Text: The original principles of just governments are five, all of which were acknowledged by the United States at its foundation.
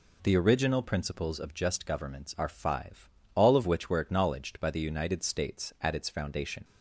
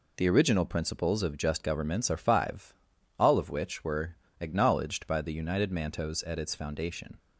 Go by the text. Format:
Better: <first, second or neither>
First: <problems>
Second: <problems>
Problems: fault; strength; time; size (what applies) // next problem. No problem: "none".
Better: first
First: none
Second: pauses between "were" and "acknowledged"; slight; at 4.1 s; 0.24 s long // says "Mantos" for "States"; at 5.7 s